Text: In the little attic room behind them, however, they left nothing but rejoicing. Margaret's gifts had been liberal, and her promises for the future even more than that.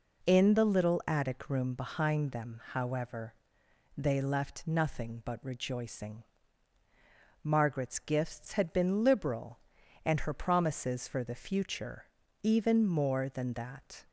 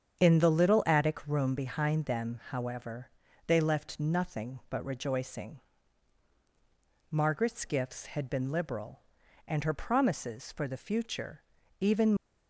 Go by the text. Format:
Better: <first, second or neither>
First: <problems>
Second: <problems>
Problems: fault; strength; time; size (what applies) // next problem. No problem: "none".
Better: first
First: pauses between "future" and "even"; at 12.0 s; 0.40 s long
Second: starts louder than the rest; strong; until 1.2 s; 8 dB // pauses between "future" and "even"; at 11.4 s; 0.38 s long // stops before "more than that"; at 12.1 s